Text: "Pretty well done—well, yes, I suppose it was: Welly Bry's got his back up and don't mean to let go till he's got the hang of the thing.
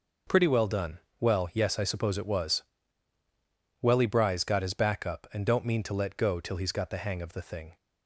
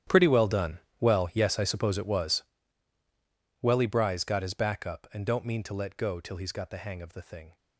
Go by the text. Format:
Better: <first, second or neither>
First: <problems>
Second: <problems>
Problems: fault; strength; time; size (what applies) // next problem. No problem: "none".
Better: first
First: none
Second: gets quieter; strong; throughout; 18.5 dB